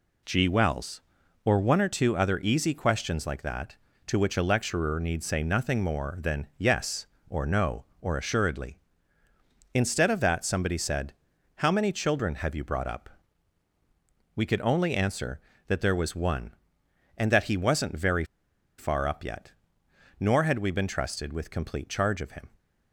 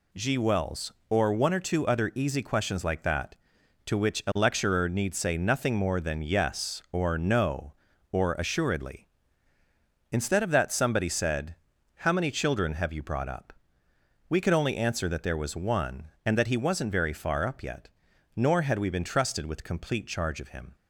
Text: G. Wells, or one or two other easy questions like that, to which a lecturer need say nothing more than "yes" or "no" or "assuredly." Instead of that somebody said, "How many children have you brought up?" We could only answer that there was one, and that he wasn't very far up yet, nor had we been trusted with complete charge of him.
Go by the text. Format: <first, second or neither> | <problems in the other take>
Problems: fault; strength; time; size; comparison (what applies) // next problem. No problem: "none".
second | pauses between "very" and "far"; noticeable; at 18.2 s; 0.54 s long